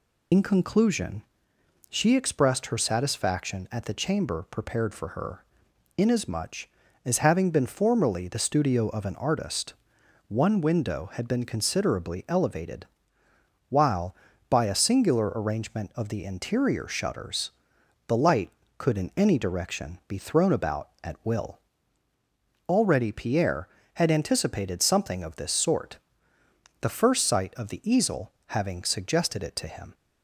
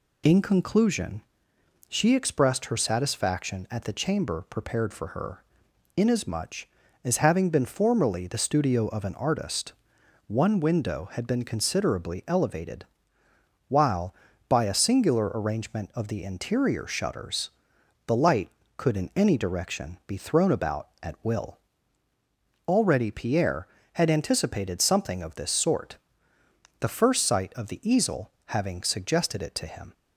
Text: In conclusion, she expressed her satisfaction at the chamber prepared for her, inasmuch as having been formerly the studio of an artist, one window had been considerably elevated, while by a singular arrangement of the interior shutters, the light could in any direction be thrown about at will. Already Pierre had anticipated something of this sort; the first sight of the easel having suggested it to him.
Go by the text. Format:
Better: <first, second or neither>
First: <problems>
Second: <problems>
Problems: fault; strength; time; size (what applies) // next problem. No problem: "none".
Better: second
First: loses the start of "In"; at 0.3 s; 75 ms // pauses between "easel" and "having"; slight; at 28.3 s; 0.16 s long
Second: pauses between "easel" and "having"; slight; at 28.3 s; 0.16 s long